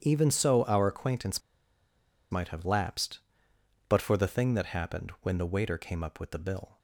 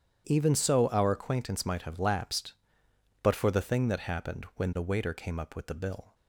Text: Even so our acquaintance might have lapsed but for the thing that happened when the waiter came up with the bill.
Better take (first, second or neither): second